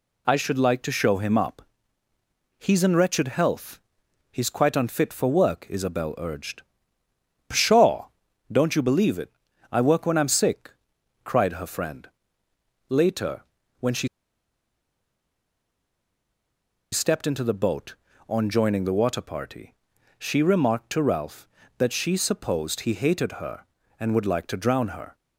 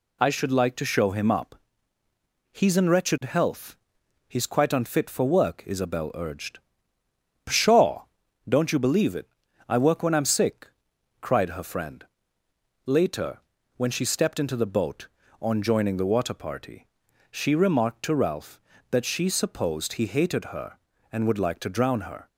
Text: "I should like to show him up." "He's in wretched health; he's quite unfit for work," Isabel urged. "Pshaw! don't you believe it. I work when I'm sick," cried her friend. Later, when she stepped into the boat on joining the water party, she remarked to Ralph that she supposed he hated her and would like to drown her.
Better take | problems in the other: second | pauses between "she" and "stepped"; strong; at 14.0 s; 2.8 s long

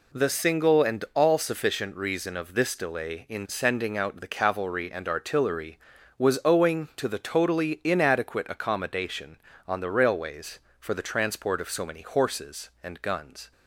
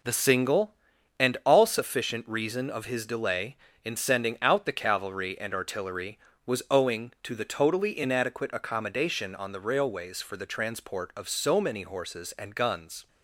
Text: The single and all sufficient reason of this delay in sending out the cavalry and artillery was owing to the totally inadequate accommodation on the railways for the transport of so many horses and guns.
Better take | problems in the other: first | says "his" for "this"; at 2.8 s

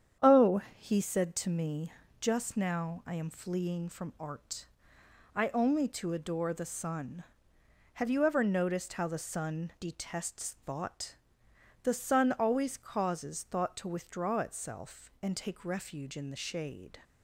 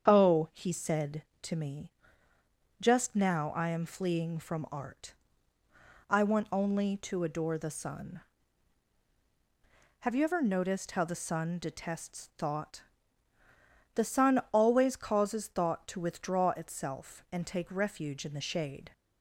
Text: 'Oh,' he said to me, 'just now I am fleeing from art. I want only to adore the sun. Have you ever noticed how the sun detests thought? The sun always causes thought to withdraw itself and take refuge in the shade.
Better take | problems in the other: second | starts louder than the rest; strong; until 1.3 s; 8.5 dB; strong in the second // skips "want"; at 5.4 s

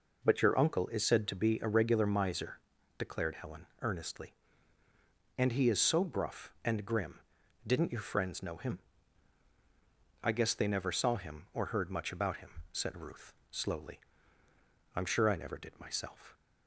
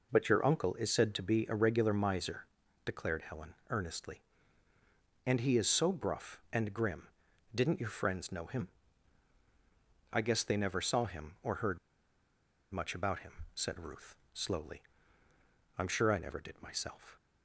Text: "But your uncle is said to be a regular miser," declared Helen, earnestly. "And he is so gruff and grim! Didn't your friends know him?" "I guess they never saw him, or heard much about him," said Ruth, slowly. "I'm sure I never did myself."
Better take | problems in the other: first | pauses between "heard" and "much"; noticeable; at 11.7 s; 0.93 s long

